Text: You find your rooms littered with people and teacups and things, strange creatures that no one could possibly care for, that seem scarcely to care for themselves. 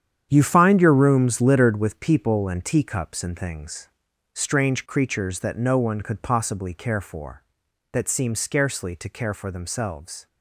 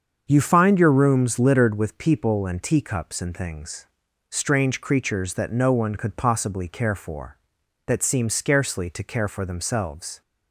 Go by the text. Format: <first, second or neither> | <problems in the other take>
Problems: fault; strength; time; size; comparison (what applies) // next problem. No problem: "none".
second | gets quieter; strong; throughout; 11.5 dB // starts louder than the rest; strong; until 1.3 s; 9 dB; also in the second